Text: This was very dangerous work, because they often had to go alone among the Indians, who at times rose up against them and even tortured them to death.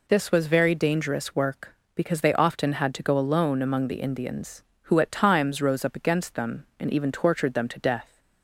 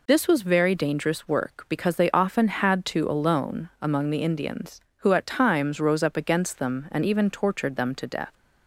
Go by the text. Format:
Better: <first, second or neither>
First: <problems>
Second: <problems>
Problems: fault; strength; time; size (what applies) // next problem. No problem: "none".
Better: first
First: none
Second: skips "go"; at 3.0 s